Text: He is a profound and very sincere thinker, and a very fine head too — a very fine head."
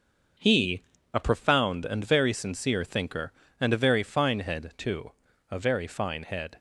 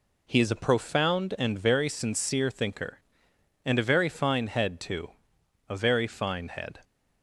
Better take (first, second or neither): second